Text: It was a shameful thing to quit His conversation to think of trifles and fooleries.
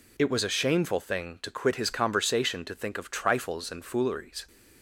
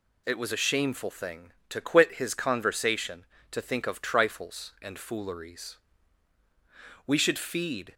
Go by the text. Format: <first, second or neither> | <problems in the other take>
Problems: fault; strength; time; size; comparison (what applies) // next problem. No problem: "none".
first | goes on to say "We should feed"; noticeable; from 7.0 s on; 0.88 s long